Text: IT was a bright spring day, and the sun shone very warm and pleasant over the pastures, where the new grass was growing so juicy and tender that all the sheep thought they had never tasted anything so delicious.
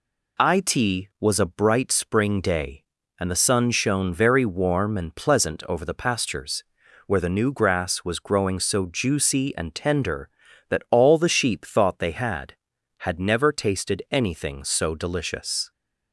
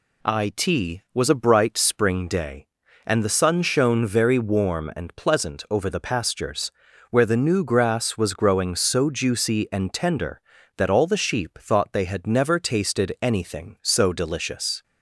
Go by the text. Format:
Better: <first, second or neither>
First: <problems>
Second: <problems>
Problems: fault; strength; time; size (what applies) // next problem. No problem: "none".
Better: second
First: says "had" twice; at 12.9 s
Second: none